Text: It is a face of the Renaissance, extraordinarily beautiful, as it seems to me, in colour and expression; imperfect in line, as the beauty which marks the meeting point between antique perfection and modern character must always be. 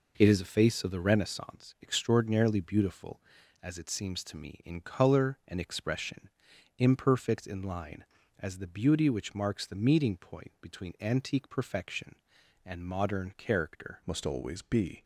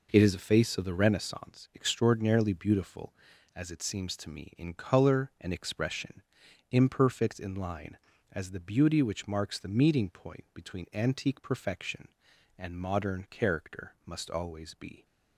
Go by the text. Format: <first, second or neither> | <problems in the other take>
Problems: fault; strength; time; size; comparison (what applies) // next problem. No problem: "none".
second | changes voice at "must"; from 14.0 s on; 1.0 s long